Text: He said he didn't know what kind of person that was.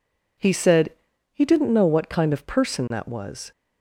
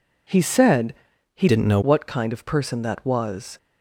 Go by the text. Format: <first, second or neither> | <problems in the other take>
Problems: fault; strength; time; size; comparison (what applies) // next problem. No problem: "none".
first | pauses between "said" and "he"; at 0.9 s; 0.42 s long; also in the first // changes voice from "didn't" to "know"; from 1.4 to 1.7 s; 0.3 s long